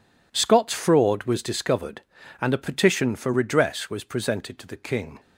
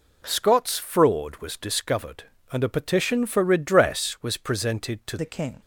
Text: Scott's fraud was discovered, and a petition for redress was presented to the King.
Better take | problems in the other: first | changes voice at "the"; from 5.1 s on; 0.5 s long

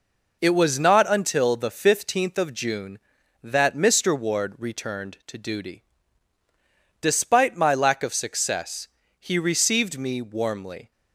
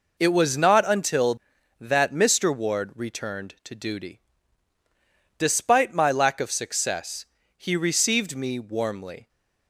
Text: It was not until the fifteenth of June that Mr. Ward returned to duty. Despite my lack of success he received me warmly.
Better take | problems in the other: first | skips "the fifteenth of June"; at 1.5 s // pauses between "success" and "he"; slight; at 7.2 s; 0.32 s long; slight in the first

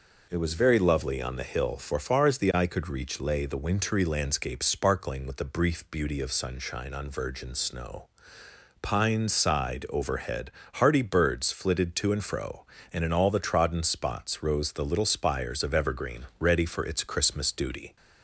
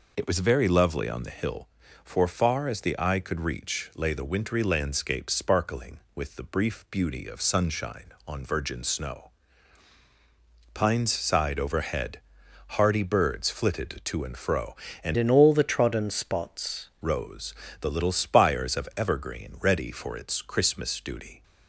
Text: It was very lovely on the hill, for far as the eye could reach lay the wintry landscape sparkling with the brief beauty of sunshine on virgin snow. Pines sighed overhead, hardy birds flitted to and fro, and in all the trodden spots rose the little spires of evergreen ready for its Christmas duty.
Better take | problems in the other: first | changes voice from "in" to "spots"; from 15.1 to 16.9 s; 1.8 s long // pauses between "rose" and "the"; slight; at 17.5 s; 0.26 s long

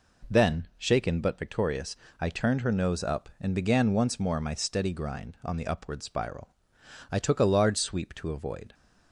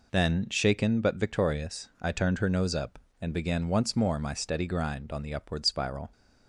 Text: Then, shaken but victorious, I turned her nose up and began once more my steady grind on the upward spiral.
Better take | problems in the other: second | goes on to say "I took a large sweep to avoid"; from 7.1 s on; 1.6 s long

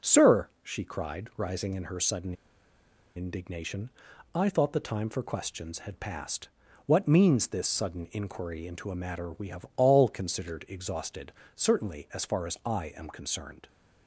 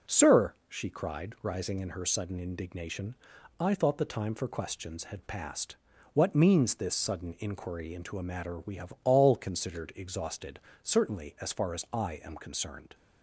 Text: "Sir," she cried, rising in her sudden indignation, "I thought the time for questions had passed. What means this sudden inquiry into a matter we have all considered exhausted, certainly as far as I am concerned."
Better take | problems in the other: second | pauses between "sudden" and "indignation"; noticeable; at 2.3 s; 0.82 s long

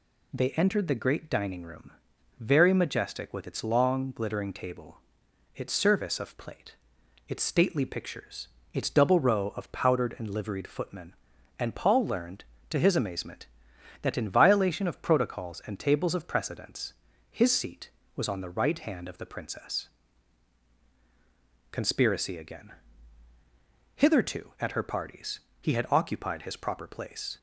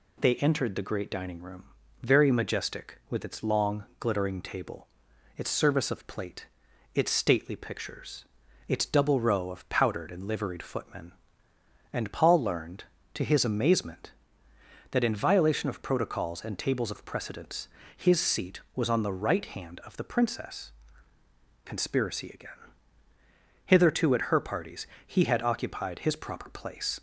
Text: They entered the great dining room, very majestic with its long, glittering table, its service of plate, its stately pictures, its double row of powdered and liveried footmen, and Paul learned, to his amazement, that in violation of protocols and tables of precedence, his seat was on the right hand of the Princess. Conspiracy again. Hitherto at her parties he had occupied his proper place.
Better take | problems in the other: neither | pauses between "parties" and "he"; slight; the same in both

